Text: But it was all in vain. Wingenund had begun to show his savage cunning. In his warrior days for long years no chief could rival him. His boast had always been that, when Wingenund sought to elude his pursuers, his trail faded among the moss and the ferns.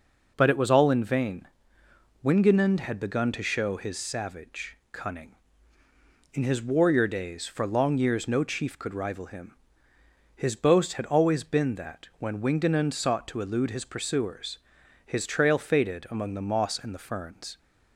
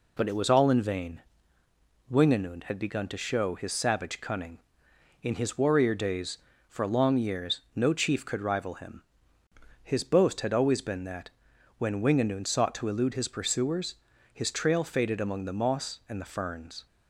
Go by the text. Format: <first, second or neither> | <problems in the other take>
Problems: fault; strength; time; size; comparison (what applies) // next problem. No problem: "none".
neither | none